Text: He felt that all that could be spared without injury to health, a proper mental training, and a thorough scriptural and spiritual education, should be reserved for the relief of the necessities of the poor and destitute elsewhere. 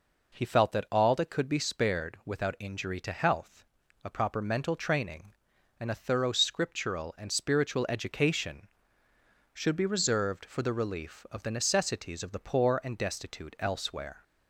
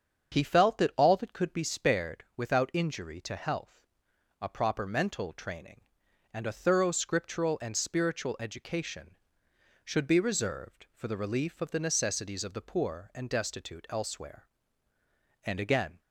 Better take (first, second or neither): first